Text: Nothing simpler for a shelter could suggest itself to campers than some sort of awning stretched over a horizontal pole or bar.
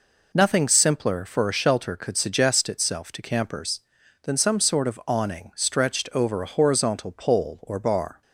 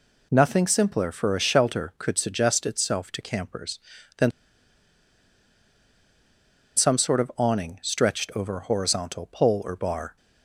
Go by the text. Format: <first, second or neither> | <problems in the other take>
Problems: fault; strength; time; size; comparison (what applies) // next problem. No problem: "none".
first | pauses between "than" and "some"; strong; at 4.3 s; 2.4 s long